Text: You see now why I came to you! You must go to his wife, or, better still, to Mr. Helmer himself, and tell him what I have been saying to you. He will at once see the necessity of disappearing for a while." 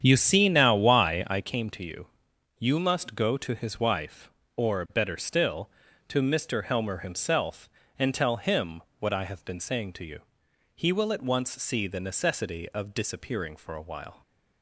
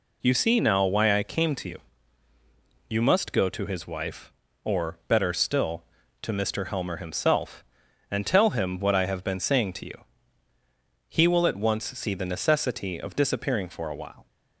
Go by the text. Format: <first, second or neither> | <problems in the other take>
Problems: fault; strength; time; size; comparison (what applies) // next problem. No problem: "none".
second | starts louder than the rest; strong; until 1.4 s; 8.5 dB // pauses between "him" and "what"; slight; at 8.8 s; 0.16 s long